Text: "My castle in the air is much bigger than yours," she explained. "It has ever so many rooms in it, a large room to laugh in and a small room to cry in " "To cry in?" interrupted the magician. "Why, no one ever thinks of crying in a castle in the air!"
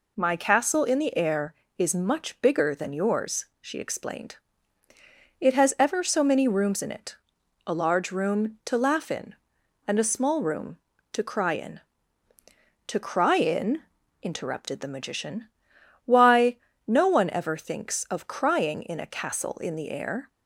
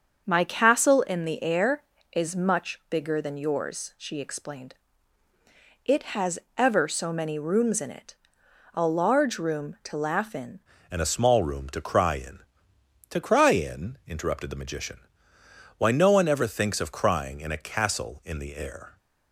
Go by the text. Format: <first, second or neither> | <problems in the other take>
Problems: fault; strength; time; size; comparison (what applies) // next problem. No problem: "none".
first | starts louder than the rest; until 1.2 s; 7 dB // pauses between "has" and "ever"; slight; at 6.3 s; 0.18 s long // changes voice at "and"; from 10.8 s on; 8.1 s long